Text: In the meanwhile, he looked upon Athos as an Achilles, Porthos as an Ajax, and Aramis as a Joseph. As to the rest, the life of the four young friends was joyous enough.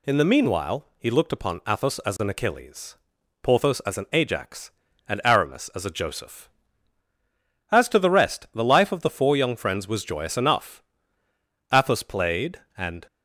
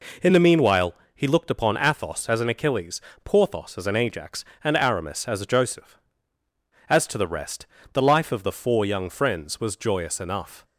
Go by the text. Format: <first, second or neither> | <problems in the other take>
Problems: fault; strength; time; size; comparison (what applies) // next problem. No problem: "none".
second | goes on to say "Athos played and"; from 11.7 s on; 1.3 s long